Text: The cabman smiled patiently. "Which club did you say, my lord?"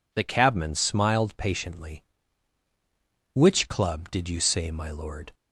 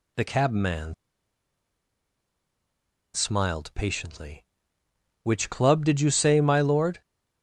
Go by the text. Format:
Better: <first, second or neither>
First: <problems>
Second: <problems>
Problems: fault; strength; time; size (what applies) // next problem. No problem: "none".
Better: first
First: none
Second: pauses between "cabman" and "smiled"; strong; at 0.9 s; 2.2 s long